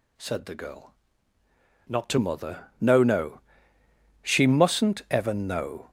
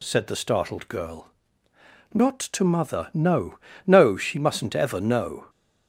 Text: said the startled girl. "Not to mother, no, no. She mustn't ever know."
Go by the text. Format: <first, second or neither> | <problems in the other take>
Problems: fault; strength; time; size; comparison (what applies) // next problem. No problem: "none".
second | skips "startled"; at 0.5 s